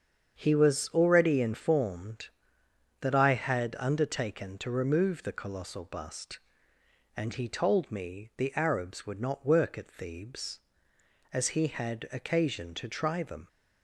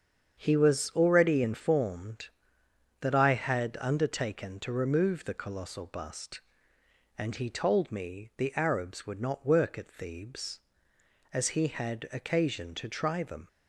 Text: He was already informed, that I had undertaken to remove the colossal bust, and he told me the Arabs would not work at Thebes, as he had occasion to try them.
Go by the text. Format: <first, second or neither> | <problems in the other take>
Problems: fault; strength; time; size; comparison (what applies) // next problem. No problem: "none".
neither | starts louder than the rest; strong; the same in both